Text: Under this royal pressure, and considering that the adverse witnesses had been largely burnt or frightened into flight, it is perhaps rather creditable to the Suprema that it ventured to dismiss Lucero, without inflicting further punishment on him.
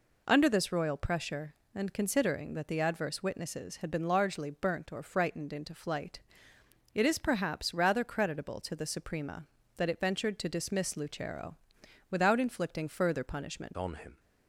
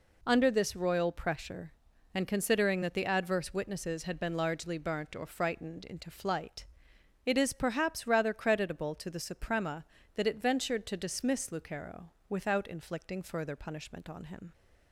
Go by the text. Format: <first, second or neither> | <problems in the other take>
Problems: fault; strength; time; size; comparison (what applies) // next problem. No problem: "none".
second | changes voice at "on"; from 13.7 s on; 0.4 s long